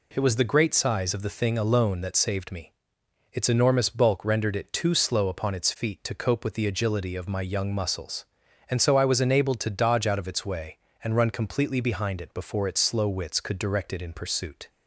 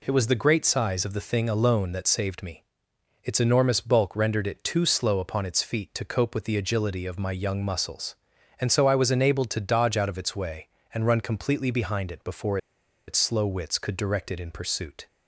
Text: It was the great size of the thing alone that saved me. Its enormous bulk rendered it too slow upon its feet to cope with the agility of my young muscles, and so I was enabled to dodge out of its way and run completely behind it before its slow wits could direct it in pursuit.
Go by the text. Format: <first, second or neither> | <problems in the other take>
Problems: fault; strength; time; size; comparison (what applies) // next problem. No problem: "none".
first | pauses between "before" and "its"; noticeable; at 12.5 s; 0.50 s long